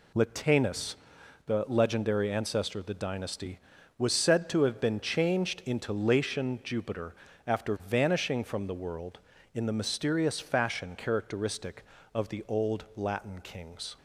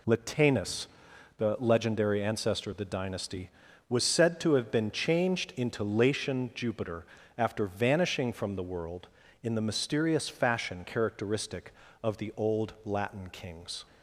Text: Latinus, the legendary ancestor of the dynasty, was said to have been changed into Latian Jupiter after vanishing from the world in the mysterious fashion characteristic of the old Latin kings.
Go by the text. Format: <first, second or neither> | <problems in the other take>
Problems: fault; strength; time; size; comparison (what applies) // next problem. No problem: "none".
neither | pauses between "Jupiter" and "after"; slight; the same in both